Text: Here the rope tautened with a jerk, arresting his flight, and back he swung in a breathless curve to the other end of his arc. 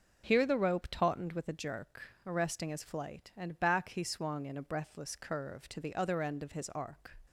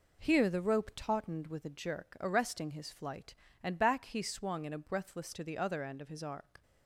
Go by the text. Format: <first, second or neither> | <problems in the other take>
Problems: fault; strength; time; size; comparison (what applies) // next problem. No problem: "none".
first | skips "curve"; at 5.3 s